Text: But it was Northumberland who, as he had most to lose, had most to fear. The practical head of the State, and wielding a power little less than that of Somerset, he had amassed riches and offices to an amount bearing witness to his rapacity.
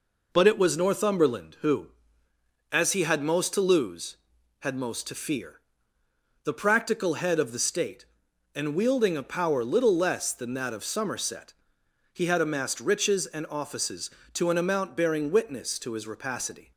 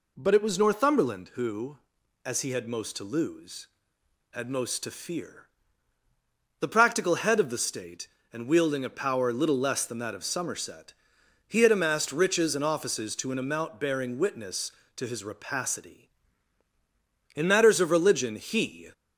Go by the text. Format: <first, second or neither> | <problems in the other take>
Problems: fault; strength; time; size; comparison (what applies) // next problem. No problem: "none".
first | goes on to say "In matters of religion he"; from 17.3 s on; 1.5 s long